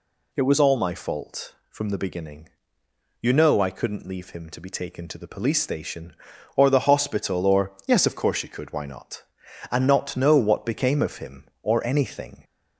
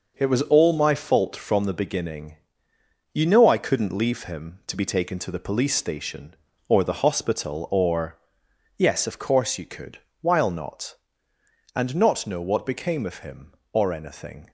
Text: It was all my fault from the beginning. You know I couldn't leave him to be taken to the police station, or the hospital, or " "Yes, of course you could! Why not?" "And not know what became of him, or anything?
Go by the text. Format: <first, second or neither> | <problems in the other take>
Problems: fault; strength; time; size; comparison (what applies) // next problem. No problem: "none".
first | says "While" for "Why"; at 10.2 s